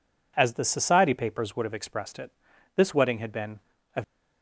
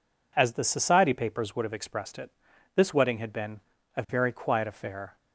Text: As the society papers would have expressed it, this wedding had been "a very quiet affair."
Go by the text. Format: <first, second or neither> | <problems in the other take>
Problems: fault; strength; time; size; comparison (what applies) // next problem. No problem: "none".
second | pauses between "been" and "a"; slight; at 3.5 s; 0.36 s long; slight in the second // stops before "very quiet affair"; at 4.0 s